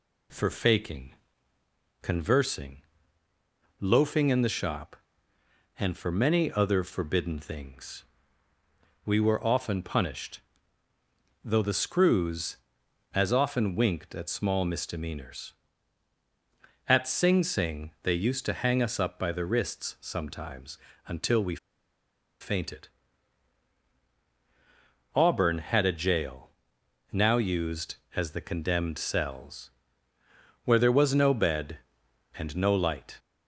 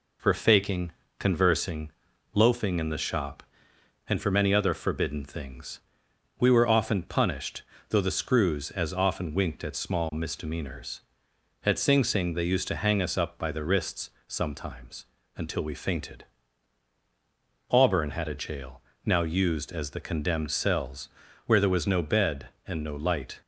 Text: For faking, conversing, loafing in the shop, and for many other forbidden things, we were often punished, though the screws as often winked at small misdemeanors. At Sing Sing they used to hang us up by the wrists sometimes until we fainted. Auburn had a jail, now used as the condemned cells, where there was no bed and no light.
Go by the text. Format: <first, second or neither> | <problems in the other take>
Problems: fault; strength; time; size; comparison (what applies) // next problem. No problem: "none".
second | pauses between "sometimes" and "until"; slight; at 20.7 s; 0.32 s long; slight in the second // pauses between "we" and "fainted"; noticeable; at 21.5 s; 0.83 s long